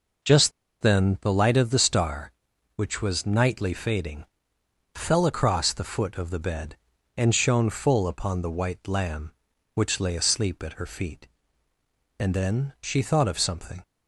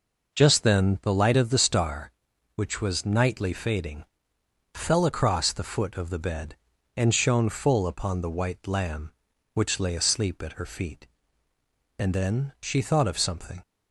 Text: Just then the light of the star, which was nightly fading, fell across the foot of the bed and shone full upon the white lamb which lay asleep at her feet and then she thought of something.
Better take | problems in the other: second | pauses between "Just" and "then"; slight; at 0.5 s; 0.29 s long

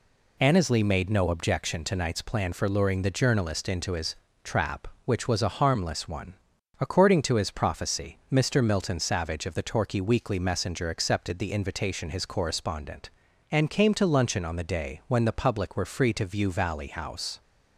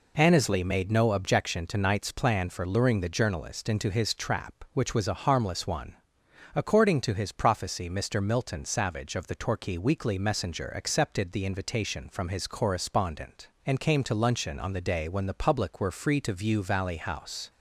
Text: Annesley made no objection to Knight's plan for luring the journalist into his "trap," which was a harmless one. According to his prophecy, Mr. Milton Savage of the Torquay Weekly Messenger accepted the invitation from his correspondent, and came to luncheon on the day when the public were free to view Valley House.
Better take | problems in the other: second | pauses between "his" and "trap"; slight; at 4.1 s; 0.30 s long // skips "from"; at 12.1 s

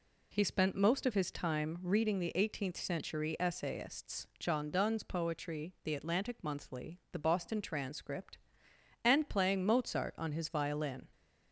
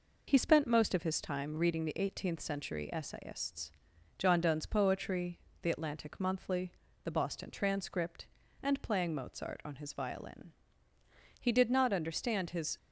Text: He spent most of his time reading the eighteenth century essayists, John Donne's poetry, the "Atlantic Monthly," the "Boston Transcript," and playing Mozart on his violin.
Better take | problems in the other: first | goes on to say "He did not understand his"; from 11.4 s on; 1.3 s long

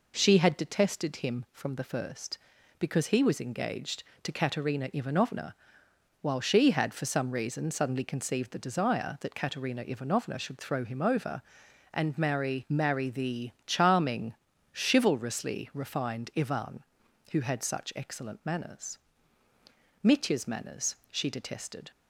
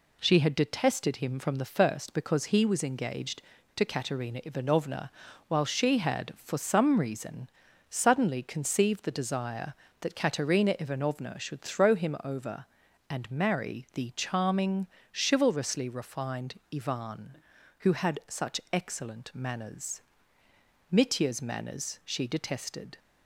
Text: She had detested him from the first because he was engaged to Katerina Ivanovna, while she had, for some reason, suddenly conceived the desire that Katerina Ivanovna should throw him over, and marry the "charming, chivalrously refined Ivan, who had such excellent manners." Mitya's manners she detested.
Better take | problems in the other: second | says "marry" twice; at 12.6 s // pauses between "the" and "charming"; slight; at 13.5 s; 0.16 s long

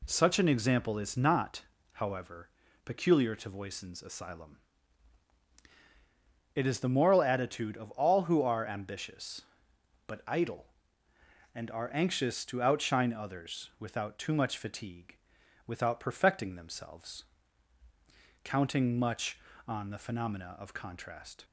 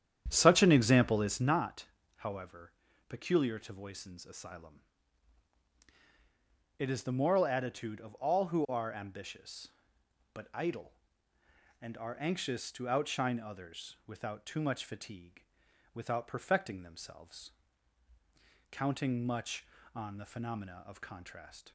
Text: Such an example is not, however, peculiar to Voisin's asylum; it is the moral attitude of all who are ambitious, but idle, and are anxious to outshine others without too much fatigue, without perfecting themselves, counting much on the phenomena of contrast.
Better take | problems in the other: first | starts louder than the rest; strong; until 1.6 s; 9.5 dB

